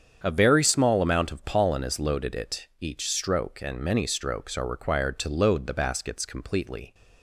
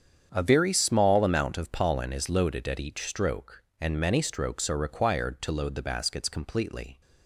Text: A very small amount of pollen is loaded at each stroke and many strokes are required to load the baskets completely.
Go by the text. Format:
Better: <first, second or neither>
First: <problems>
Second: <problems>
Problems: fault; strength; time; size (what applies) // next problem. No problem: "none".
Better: second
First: starts louder than the rest; strong; until 1.2 s; 8 dB // says "it" for "at"; at 2.3 s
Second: starts louder than the rest; strong; until 1.3 s; 8 dB